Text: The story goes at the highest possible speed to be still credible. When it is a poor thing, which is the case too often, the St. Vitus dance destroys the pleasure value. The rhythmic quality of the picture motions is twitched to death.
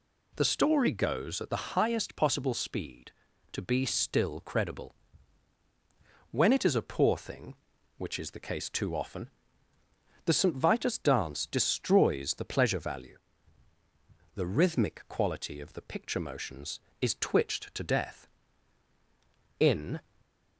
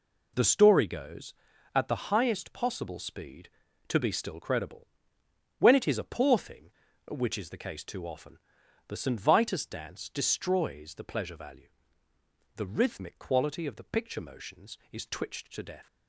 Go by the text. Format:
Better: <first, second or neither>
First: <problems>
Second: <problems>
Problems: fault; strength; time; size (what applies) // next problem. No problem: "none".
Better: second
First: goes on to say "In"; slight; from 19.5 s on; 0.40 s long // stays silent after the last word; slight; from 20.0 s on; 0.5 s long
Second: none